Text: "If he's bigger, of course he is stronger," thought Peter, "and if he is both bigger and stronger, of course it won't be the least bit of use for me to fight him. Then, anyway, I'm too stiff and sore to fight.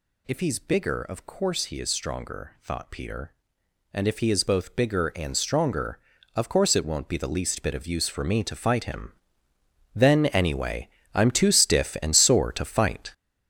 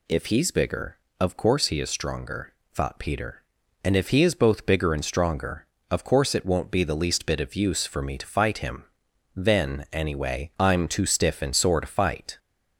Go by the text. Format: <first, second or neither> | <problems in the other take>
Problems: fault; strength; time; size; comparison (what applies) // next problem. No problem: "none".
second | gets louder; strong; throughout; 9 dB